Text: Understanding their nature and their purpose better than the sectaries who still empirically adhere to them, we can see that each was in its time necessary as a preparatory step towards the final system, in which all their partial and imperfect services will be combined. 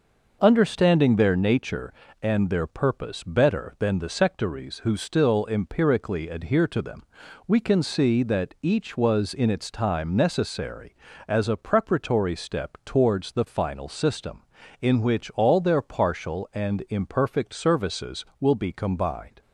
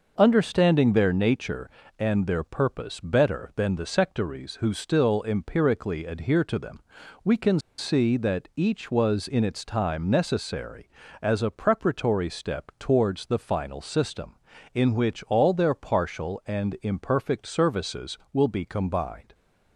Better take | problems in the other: first | pauses between "can" and "see"; slight; at 7.5 s; 0.19 s long

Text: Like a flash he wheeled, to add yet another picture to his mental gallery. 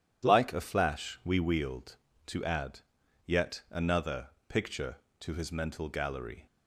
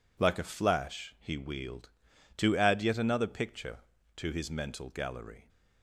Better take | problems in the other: second | says "we" for "he"; at 1.2 s // pauses between "add" and "yet"; noticeable; at 2.7 s; 0.46 s long // pauses between "another" and "picture"; slight; at 4.2 s; 0.20 s long

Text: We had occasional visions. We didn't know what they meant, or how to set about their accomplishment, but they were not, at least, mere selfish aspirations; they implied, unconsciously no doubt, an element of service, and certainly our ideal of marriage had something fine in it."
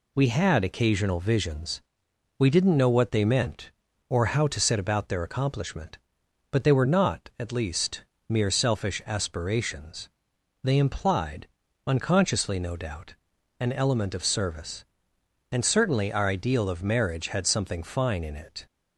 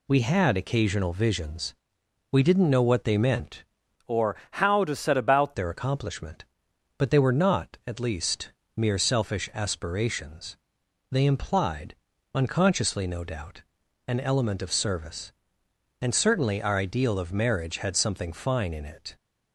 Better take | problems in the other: first | changes voice from "or" to "about"; from 4.0 to 5.5 s; 1.5 s long // pauses between "or" and "how"; slight; at 4.3 s; 0.16 s long

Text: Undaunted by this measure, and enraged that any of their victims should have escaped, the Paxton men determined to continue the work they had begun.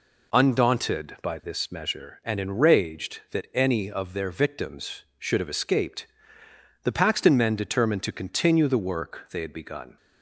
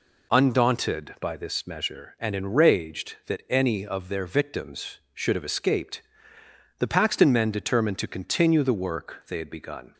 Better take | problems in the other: neither | none

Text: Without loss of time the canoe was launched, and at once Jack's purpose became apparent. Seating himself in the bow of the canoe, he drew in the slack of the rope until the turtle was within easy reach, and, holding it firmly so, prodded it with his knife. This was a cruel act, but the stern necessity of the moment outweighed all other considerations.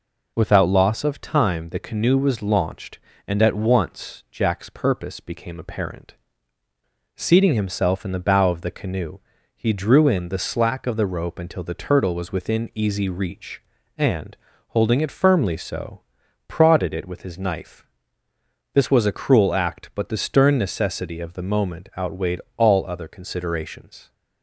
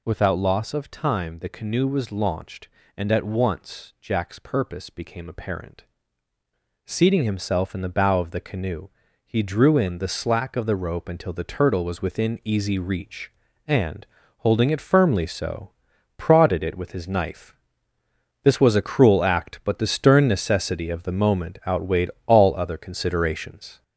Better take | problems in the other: first | gets louder; noticeable; throughout; 5 dB // pauses between "outweighed" and "all"; slight; at 22.1 s; 0.16 s long; slight in the first

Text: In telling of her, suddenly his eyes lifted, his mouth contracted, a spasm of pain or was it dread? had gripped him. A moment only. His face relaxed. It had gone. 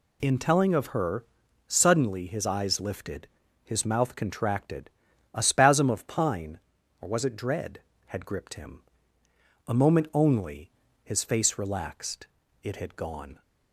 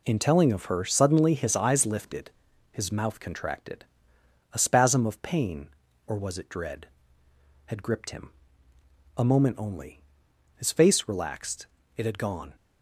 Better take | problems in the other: second | says "pine" for "pain"; at 6.0 s

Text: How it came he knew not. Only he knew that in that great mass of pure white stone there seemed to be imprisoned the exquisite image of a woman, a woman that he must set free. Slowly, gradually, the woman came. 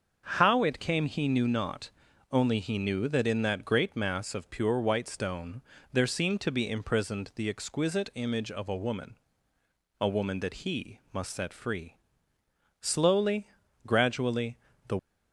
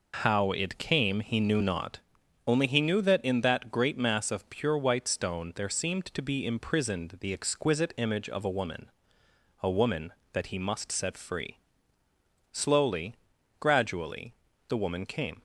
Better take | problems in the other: second | starts louder than the rest; until 1.2 s; 6.5 dB // pauses between "stone" and "there"; slight; at 5.6 s; 0.30 s long // stops before "woman came"; at 14.9 s

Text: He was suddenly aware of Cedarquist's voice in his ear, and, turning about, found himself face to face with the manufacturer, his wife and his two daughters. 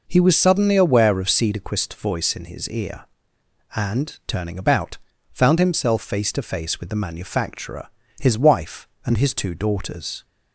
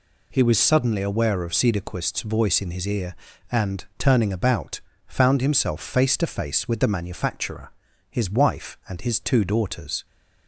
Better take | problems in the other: neither | none

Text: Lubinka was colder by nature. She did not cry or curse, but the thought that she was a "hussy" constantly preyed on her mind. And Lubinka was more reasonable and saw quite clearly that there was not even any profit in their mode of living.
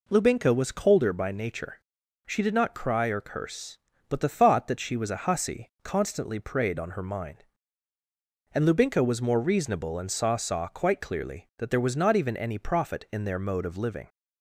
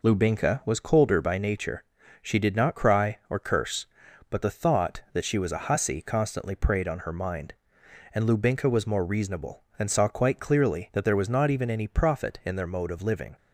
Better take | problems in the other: second | says "saw" twice; at 10.3 s

